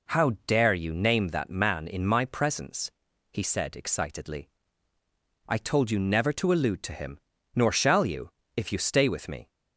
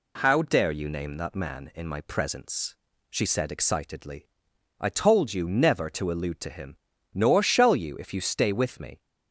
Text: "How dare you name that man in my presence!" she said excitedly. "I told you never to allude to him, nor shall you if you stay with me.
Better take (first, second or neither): second